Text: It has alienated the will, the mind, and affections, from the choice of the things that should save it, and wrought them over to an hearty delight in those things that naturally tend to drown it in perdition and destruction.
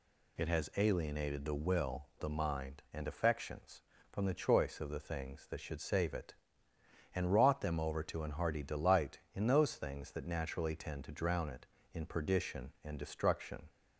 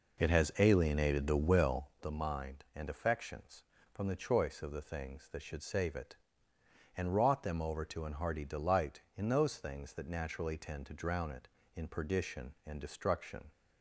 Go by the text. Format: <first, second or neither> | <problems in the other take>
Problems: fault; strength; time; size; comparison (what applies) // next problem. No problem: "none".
first | starts louder than the rest; noticeable; until 2.0 s; 4.5 dB